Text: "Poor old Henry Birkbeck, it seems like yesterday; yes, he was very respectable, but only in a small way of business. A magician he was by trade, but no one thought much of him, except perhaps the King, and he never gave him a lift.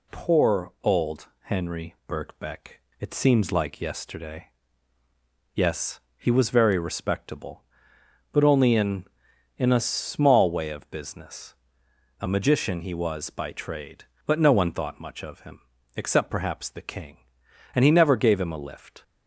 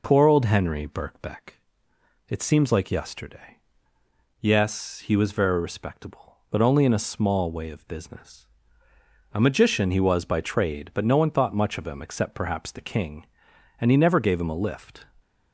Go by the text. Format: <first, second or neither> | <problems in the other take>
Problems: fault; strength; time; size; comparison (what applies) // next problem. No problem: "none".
second | says "in" twice; at 9.5 s